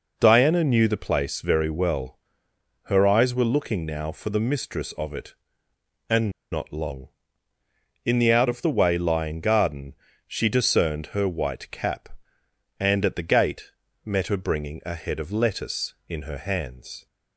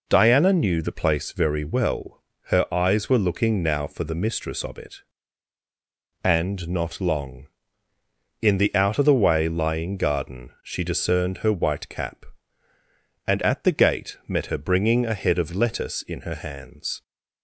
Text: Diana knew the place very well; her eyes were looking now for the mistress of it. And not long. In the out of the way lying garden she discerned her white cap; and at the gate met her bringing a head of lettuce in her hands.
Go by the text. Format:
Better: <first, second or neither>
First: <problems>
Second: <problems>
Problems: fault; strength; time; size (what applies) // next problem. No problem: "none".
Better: second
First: pauses between "And" and "not"; slight; at 6.3 s; 0.21 s long // pauses between "garden" and "she"; slight; at 9.9 s; 0.32 s long // pauses between "gate" and "met"; slight; at 13.7 s; 0.34 s long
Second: none